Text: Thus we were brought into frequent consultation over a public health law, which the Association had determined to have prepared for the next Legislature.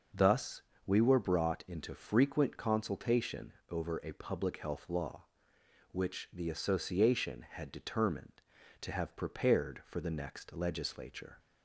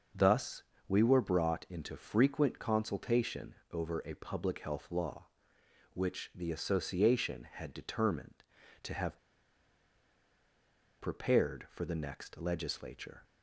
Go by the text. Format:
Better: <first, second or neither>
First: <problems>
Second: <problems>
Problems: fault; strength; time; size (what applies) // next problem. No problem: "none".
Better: first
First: starts louder than the rest; noticeable; until 1.3 s; 6 dB // pauses between "Thus" and "we"; slight; at 0.6 s; 0.25 s long // pauses between "consultation" and "over"; slight; at 3.5 s; 0.16 s long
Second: starts louder than the rest; noticeable; until 1.4 s; 6 dB // pauses between "Thus" and "we"; slight; at 0.6 s; 0.26 s long // pauses between "consultation" and "over"; slight; at 3.5 s; 0.16 s long // pauses between "have" and "prepared"; strong; at 9.1 s; 1.8 s long